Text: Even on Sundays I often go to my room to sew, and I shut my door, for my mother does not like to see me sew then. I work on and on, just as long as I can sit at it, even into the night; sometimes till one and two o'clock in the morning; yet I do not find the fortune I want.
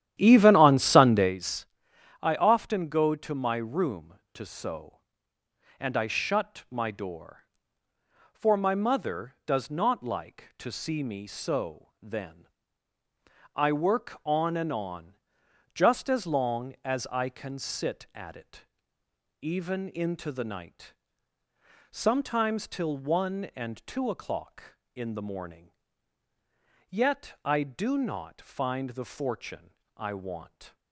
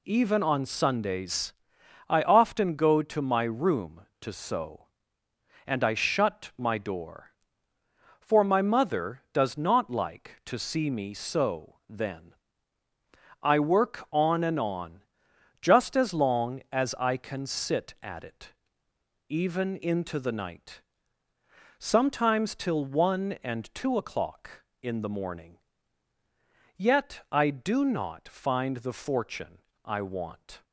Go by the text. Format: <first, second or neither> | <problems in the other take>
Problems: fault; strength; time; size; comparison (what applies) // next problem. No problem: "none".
second | starts louder than the rest; strong; until 1.4 s; 11.5 dB // pauses between "Sundays" and "I"; noticeable; at 1.6 s; 0.54 s long; noticeable in the second // pauses between "fortune" and "I"; slight; at 29.7 s; 0.26 s long; slight in the second